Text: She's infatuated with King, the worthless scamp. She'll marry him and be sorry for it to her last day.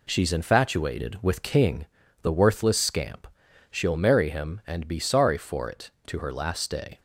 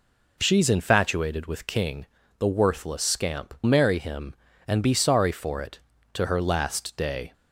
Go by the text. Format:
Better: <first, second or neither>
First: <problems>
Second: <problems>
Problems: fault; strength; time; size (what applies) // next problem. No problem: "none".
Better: first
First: none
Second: skips "She'll"; at 3.5 s